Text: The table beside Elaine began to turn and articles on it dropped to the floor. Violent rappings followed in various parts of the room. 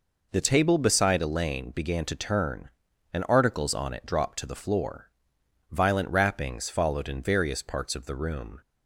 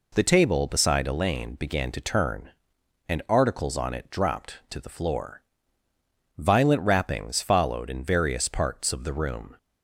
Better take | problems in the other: neither | none

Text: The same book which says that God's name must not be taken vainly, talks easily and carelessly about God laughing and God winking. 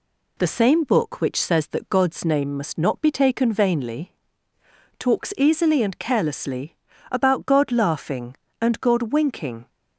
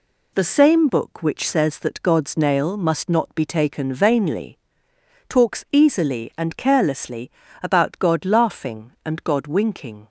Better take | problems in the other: first | says "nail" for "name"; at 2.3 s // pauses between "carelessly" and "about"; slight; at 7.3 s; 0.32 s long; slight in the first

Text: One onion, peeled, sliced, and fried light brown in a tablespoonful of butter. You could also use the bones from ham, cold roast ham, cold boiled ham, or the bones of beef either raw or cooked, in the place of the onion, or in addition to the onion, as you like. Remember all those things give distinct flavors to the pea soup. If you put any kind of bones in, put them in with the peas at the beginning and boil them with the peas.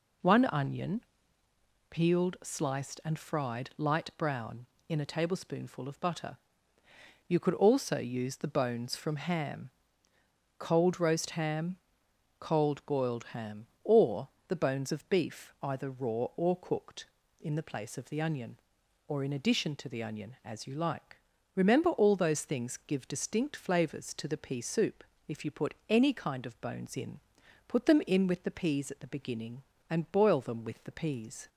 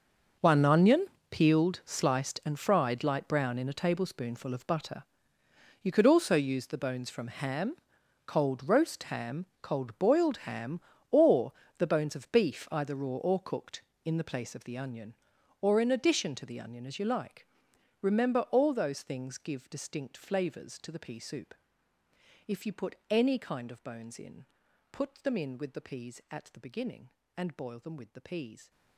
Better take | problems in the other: first | gets quieter; strong; throughout; 16 dB // pauses between "or" and "the"; slight; at 11.5 s; 0.26 s long; slight in the first

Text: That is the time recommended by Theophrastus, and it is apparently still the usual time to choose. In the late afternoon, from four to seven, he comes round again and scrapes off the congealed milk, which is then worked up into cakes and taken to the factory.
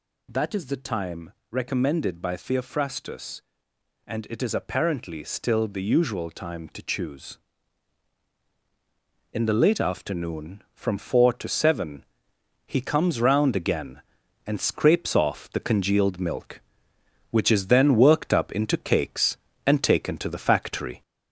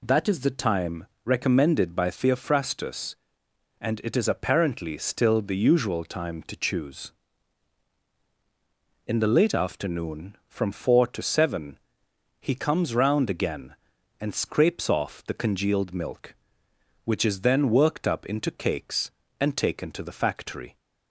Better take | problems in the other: second | gets louder; throughout; 4 dB // pauses between "time" and "recommended"; slight; at 1.3 s; 0.18 s long; slight in the second

